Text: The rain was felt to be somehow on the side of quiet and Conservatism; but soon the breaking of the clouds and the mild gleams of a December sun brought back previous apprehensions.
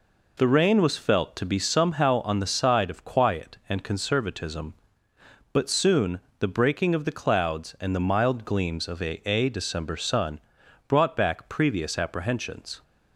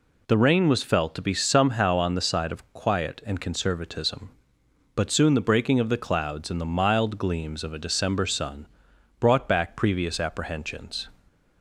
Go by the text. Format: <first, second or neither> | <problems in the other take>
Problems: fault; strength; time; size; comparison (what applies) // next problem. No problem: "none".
second | pauses between "soon" and "the"; slight; at 6.2 s; 0.18 s long // says "a" twice; at 9.2 s // pauses between "sun" and "brought"; noticeable; at 10.3 s; 0.48 s long; noticeable in the second